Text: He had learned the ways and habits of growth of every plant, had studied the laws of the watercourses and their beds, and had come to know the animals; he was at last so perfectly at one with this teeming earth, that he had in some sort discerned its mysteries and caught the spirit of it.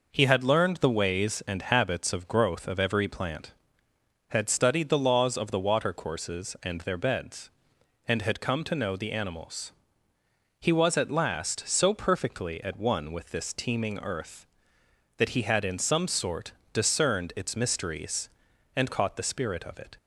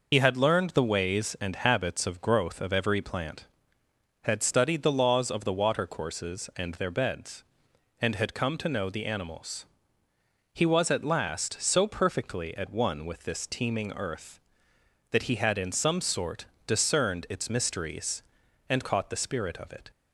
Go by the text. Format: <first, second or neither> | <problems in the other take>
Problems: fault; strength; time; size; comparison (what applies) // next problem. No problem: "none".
first | loses the start of "He"; at 0.1 s; 60 ms // pauses between "sort" and "discerned"; slight; at 16.4 s; 0.22 s long; slight in the first